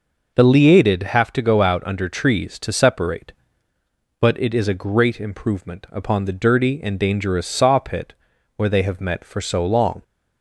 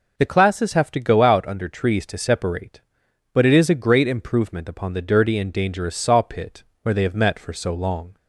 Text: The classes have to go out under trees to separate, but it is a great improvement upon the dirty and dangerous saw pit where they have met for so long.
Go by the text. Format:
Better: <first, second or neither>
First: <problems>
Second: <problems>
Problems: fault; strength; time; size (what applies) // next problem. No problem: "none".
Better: second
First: says "liated" for "classes"; at 0.4 s // pauses between "pit" and "where"; at 8.1 s; 0.42 s long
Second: pauses between "pit" and "where"; slight; at 6.6 s; 0.18 s long